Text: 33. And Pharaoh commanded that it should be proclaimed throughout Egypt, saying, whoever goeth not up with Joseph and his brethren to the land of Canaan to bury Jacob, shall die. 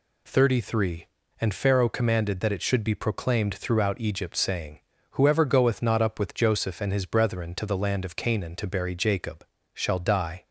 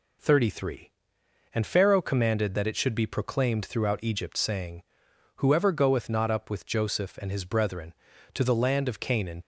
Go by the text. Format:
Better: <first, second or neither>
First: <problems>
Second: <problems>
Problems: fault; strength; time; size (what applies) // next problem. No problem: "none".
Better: first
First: none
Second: stops before "to bury Jacob shall die"; at 9.4 s